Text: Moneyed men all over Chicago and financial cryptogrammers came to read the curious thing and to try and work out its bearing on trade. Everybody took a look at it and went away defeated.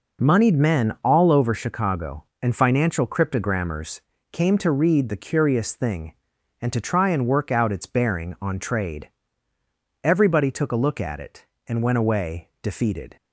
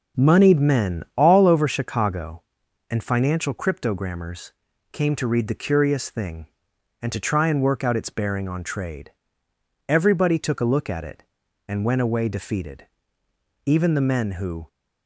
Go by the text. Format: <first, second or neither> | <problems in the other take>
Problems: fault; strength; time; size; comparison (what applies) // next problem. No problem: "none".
first | starts louder than the rest; until 1.3 s; 6.5 dB // pauses between "cryptogrammers" and "came"; at 4.5 s; 0.42 s long; slight in the first // goes on to say "Even the men who"; noticeable; from 13.6 s on; 1.0 s long